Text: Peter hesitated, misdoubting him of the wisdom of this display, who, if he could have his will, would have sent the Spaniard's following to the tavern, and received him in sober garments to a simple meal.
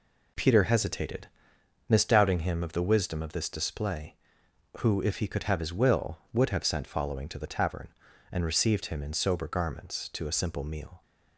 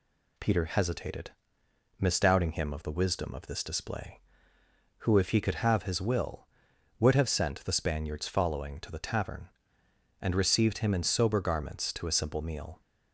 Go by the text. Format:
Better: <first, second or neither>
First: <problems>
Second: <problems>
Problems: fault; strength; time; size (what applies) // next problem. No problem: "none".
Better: second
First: skips "the Spaniard's"; at 6.8 s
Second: none